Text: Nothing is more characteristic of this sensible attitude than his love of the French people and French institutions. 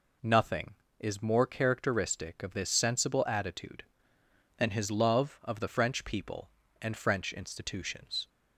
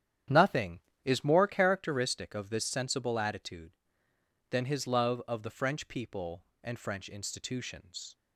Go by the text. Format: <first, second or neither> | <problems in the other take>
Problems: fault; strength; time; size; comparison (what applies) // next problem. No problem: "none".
first | starts louder than the rest; strong; until 1.7 s; 9.5 dB